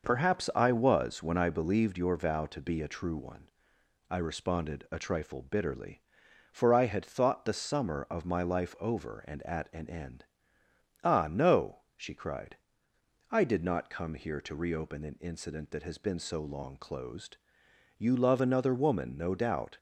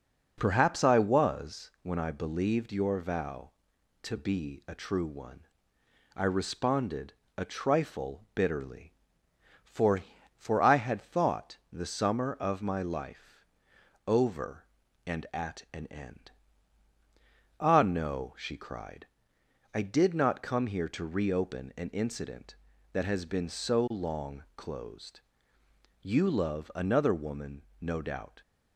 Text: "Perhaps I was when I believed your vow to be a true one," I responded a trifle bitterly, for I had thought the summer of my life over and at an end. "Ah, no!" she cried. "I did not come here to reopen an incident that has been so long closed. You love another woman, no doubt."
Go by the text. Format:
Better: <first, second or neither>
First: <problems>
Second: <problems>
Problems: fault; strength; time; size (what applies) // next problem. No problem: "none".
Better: first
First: none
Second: pauses between "responded" and "a"; slight; at 7.1 s; 0.26 s long // says "for" twice; at 10.3 s // pauses between "thought" and "the"; slight; at 11.5 s; 0.16 s long // pauses between "life" and "over"; noticeable; at 13.4 s; 0.64 s long